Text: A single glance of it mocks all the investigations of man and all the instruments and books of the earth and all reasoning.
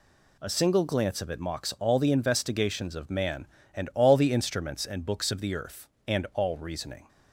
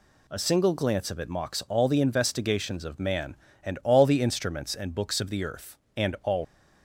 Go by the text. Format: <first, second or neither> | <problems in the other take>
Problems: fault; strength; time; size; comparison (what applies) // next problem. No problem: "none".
first | stops before "reasoning"; at 6.4 s